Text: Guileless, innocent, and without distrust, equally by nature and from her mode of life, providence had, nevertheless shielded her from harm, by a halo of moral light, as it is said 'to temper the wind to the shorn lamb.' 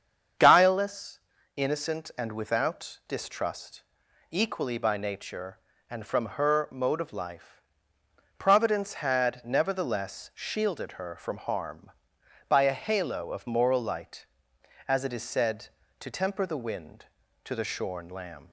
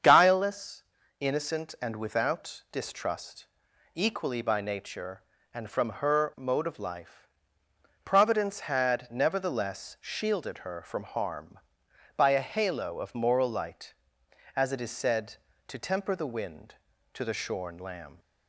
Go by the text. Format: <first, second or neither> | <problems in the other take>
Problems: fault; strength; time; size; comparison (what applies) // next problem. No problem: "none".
neither | starts louder than the rest; strong; the same in both